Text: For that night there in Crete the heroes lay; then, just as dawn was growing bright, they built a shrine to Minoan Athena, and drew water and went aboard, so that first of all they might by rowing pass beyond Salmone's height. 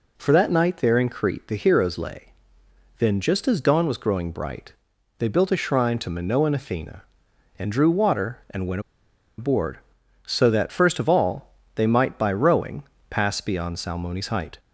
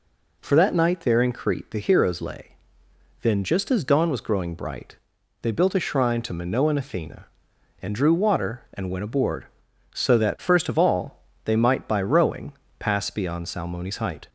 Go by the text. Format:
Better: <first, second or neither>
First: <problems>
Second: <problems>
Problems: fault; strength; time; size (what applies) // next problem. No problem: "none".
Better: second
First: pauses between "went" and "aboard"; noticeable; at 8.8 s; 0.56 s long // pauses between "all" and "they"; slight; at 11.5 s; 0.18 s long // pauses between "rowing" and "pass"; slight; at 12.8 s; 0.26 s long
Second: pauses between "all" and "they"; slight; at 11.2 s; 0.18 s long // pauses between "rowing" and "pass"; slight; at 12.5 s; 0.26 s long